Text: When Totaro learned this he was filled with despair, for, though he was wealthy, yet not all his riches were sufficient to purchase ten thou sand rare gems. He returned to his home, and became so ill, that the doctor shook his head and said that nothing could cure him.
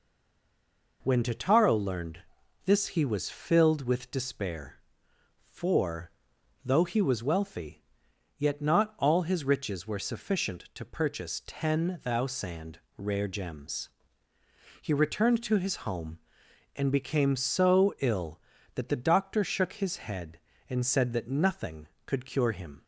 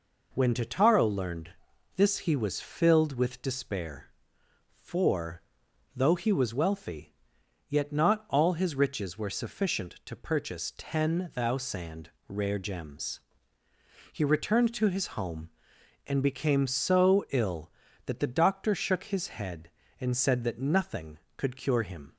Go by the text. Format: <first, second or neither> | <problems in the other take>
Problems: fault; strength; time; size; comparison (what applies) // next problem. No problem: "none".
second | stays silent before the first word; until 1.0 s; 1.0 s long // pauses between "learned" and "this"; noticeable; at 2.1 s; 0.46 s long; noticeable in the second // pauses between "sand" and "rare"; slight; at 12.7 s; 0.20 s long; slight in the second